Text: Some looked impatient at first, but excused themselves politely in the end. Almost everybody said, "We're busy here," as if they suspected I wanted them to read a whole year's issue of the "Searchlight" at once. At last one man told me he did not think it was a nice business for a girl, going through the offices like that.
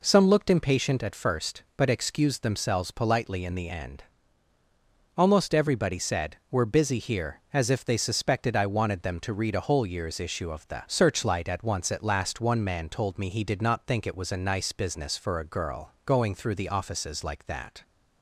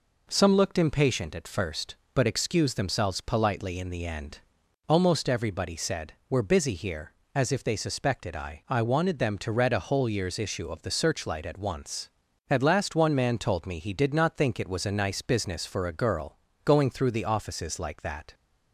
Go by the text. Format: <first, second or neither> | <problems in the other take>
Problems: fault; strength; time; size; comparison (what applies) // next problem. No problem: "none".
first | says "I" twice; at 8.6 s